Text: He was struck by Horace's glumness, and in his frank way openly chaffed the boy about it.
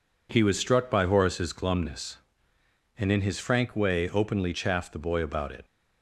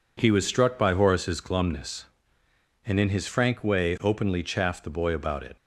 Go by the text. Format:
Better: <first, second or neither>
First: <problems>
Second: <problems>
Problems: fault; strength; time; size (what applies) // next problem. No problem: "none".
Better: neither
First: none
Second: none